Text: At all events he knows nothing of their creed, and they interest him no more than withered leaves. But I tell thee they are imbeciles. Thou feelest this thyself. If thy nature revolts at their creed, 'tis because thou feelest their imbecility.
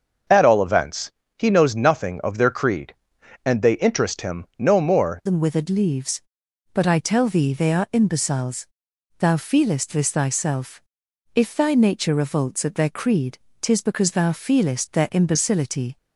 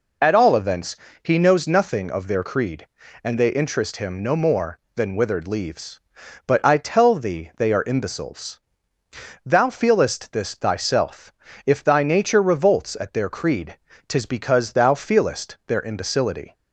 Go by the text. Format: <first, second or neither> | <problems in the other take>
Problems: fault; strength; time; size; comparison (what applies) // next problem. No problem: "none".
second | starts louder than the rest; until 1.5 s; 6.5 dB // pauses between "events" and "he"; slight; at 1.1 s; 0.26 s long; slight in the second // changes voice at "than"; from 5.2 s on; 10.7 s long